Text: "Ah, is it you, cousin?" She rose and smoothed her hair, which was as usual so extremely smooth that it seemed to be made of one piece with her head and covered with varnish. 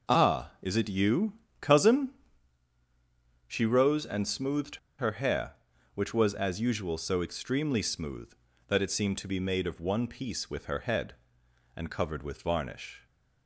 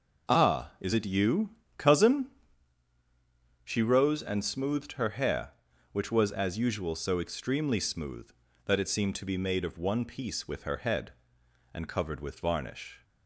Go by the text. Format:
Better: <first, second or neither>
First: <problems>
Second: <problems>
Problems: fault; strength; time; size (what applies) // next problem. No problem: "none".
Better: second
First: pauses between "smoothed" and "her"; slight; at 4.7 s; 0.21 s long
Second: none